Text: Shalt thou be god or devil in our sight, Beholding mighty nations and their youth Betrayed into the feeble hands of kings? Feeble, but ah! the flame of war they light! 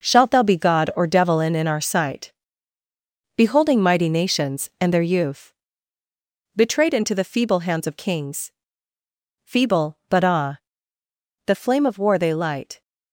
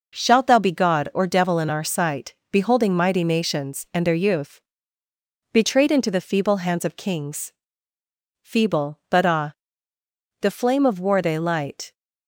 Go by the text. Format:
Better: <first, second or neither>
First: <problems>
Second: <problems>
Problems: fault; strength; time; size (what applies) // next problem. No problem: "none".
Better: second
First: says "in" twice; at 1.5 s // pauses between "youth" and "Betrayed"; at 5.5 s; 1.0 s long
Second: pauses between "youth" and "Betrayed"; noticeable; at 4.5 s; 0.92 s long